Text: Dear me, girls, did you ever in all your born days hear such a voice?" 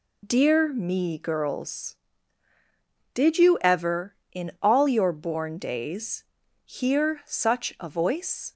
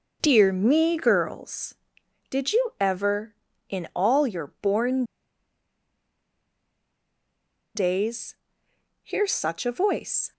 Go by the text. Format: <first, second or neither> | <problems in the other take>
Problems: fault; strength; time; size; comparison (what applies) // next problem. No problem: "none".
first | pauses between "born" and "days"; strong; at 5.0 s; 2.7 s long // pauses between "days" and "hear"; noticeable; at 8.3 s; 0.70 s long; also in the first